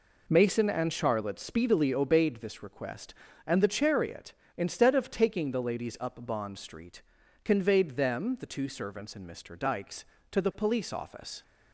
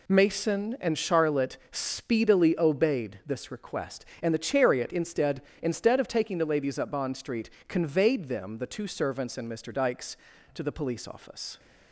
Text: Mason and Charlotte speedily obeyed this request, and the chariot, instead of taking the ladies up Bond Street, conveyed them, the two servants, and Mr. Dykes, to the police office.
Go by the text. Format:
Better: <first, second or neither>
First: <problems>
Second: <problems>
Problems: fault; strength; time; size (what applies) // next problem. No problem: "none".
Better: first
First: none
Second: says "instead" twice; at 5.6 s